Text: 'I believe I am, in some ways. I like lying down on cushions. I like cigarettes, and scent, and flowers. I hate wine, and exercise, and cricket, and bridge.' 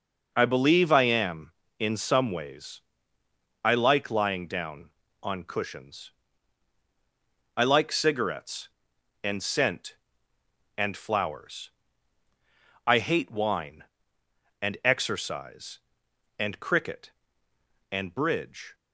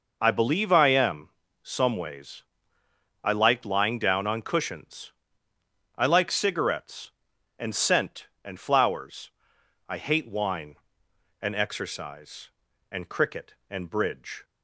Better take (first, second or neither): first